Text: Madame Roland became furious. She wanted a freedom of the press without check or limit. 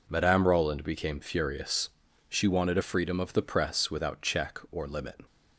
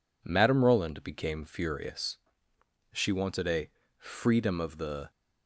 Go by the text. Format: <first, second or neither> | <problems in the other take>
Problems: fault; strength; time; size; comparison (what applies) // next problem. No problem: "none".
first | pauses between "a" and "freedom"; slight; at 3.7 s; 0.28 s long // stops before "press without check or limit"; at 5.1 s